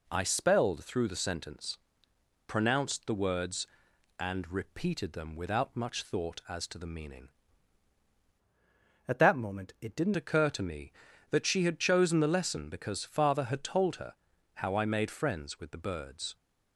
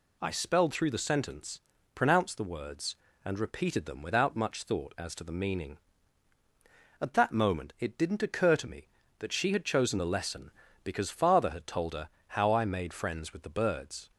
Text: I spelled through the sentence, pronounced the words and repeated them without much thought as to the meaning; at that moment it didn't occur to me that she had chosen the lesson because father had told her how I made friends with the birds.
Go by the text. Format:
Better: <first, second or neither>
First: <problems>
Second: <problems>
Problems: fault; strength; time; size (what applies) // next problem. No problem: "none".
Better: second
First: changes voice from "at" to "didn't"; from 9.0 to 10.1 s; 1.1 s long // pauses between "her" and "how"; at 14.1 s; 0.40 s long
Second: pauses between "her" and "how"; slight; at 12.0 s; 0.18 s long